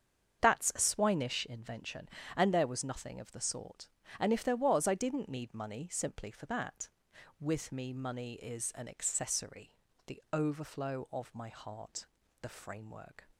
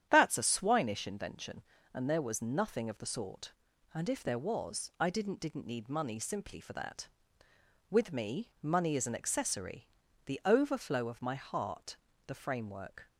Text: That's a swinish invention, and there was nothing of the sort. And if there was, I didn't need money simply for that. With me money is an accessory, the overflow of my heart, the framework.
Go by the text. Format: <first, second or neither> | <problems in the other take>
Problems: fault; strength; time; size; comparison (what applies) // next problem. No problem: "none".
first | starts louder than the rest; strong; until 1.1 s; 9.5 dB; strong in the first // says "didn't" twice; at 5.3 s